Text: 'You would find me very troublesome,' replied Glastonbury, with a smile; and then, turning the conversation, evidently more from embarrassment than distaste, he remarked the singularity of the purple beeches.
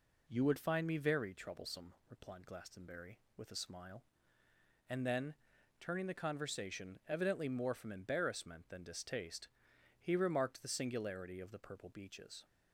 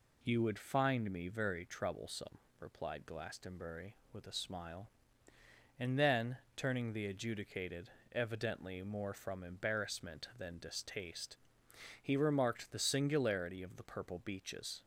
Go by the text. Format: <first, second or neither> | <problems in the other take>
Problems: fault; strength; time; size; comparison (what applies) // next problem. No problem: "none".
first | says "adjudicated" for "conversation"; at 7.0 s